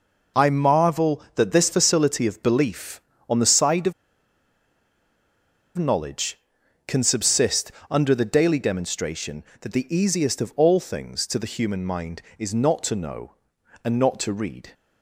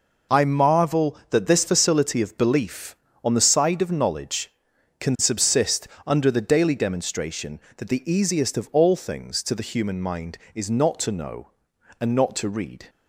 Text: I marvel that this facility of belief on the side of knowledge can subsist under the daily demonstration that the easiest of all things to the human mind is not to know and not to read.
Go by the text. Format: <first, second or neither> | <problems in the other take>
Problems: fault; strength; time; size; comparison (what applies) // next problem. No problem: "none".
second | pauses between "of" and "knowledge"; strong; at 3.9 s; 1.8 s long // pauses between "subsist" and "under"; slight; at 7.7 s; 0.20 s long; slight in the second